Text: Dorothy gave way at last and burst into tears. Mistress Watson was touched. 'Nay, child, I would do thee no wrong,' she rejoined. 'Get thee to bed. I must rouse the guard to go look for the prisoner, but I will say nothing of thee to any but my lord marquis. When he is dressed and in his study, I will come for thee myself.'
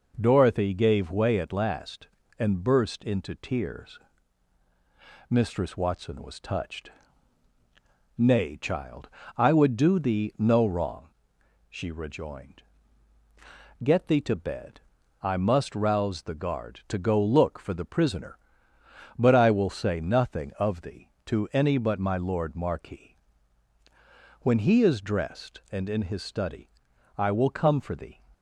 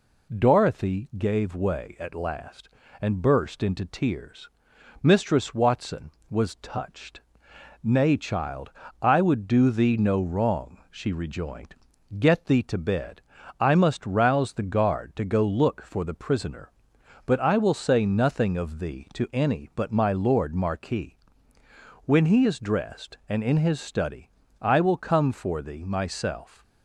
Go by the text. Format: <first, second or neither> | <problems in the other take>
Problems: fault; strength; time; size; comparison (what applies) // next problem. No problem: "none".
second | stops before "myself"; at 28.3 s